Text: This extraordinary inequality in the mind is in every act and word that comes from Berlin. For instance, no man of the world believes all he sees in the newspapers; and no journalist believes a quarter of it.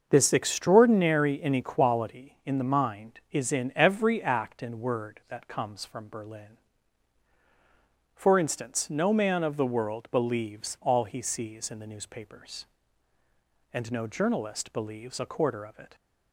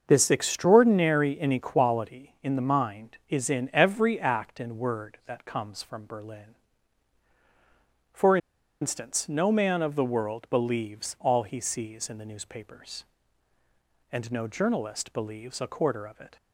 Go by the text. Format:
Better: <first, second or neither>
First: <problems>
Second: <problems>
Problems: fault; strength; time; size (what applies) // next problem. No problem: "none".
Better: first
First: starts louder than the rest; until 1.1 s; 6.5 dB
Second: starts louder than the rest; until 1.0 s; 6.5 dB // pauses between "For" and "instance"; at 8.3 s; 0.44 s long